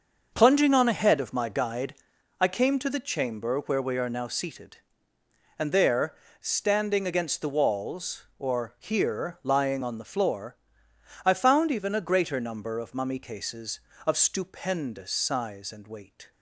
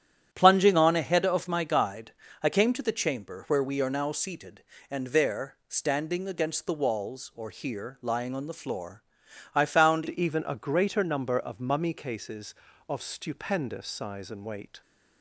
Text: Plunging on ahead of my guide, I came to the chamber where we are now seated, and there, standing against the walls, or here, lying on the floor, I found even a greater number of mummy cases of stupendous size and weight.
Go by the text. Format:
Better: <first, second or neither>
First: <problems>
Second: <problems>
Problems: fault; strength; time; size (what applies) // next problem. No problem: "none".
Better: first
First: starts louder than the rest; until 1.3 s; 6.5 dB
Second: starts louder than the rest; strong; until 1.3 s; 9.5 dB // changes voice at "even"; from 10.0 s on; 4.8 s long